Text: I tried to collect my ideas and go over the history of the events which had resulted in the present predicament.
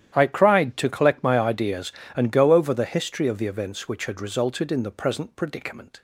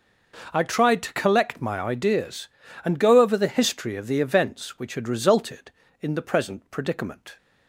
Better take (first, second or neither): second